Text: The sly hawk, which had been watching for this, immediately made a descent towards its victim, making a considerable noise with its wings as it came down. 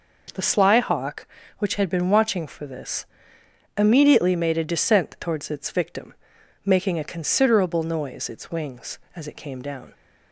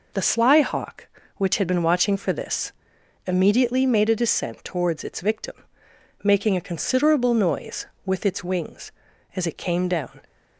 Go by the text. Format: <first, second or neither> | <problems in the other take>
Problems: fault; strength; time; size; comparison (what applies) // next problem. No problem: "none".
second | skips "with"; at 8.2 s